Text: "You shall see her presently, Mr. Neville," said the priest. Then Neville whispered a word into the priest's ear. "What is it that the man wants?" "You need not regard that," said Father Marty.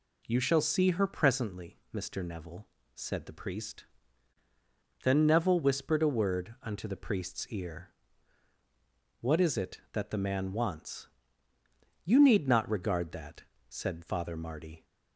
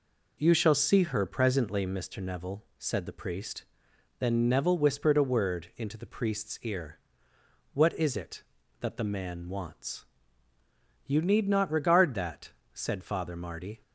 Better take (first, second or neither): second